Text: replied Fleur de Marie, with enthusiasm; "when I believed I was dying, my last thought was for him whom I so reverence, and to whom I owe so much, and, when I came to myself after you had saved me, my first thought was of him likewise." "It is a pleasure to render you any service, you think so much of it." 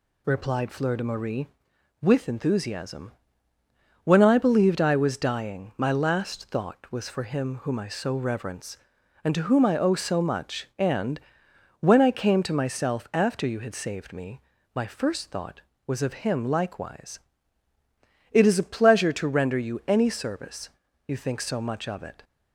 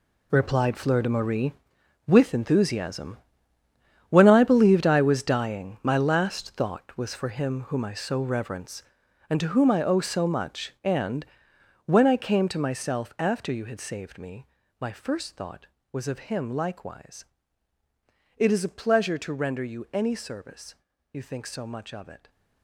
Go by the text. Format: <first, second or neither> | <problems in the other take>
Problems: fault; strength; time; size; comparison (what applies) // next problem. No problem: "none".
first | gets quieter; strong; throughout; 12.5 dB